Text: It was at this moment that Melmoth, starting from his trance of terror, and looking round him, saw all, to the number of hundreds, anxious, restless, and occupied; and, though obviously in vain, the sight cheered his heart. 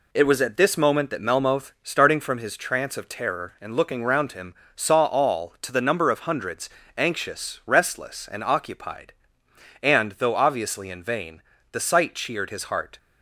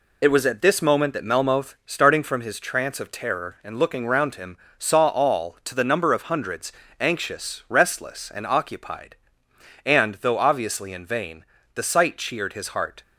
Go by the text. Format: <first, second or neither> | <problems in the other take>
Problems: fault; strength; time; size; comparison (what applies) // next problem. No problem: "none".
first | loses the start of "It"; at 0.2 s; 50 ms